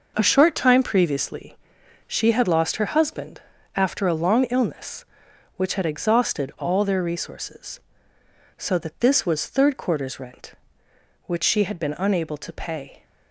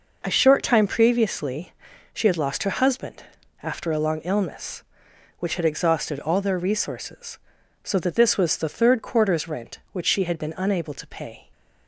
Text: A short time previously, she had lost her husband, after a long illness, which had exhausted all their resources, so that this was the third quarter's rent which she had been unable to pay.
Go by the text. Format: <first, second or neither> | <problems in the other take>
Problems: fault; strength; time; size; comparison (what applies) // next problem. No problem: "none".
second | skips "the"; at 9.4 s